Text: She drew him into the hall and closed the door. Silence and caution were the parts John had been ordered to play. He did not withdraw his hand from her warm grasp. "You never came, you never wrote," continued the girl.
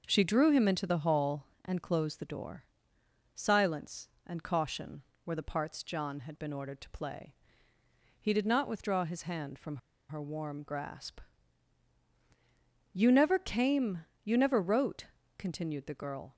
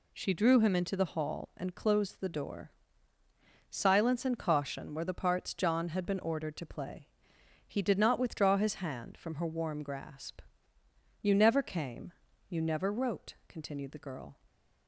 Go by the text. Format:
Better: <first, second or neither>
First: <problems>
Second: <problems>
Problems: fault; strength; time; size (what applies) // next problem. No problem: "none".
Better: second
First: starts louder than the rest; noticeable; until 1.0 s; 6 dB // pauses between "from" and "her"; slight; at 9.7 s; 0.32 s long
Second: none